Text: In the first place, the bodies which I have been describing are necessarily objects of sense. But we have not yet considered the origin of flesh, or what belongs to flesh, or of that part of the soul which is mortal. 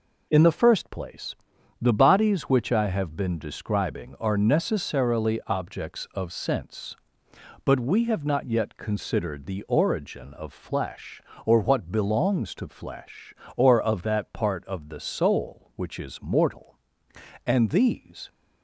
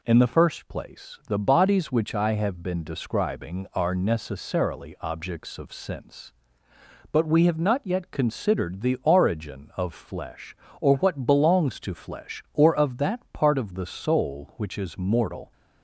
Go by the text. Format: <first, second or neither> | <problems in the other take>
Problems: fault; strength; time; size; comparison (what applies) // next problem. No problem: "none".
second | goes on to say "And these"; noticeable; from 17.4 s on; 0.82 s long